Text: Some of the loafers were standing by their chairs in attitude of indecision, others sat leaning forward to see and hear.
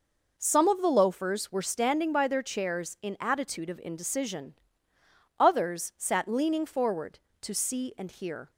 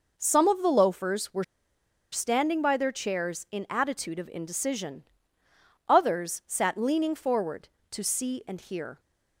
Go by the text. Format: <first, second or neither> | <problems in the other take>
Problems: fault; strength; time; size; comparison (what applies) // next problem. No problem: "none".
first | pauses between "were" and "standing"; noticeable; at 1.4 s; 0.68 s long